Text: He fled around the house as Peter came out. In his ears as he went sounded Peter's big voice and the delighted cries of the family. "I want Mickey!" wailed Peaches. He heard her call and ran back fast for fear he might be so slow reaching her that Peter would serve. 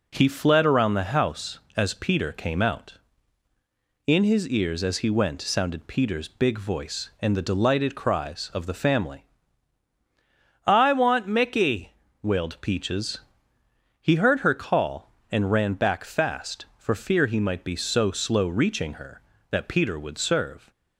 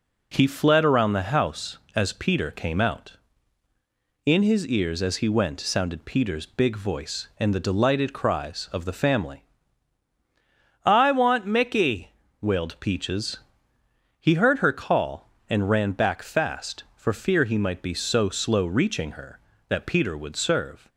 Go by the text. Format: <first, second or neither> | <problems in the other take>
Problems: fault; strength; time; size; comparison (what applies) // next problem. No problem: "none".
neither | none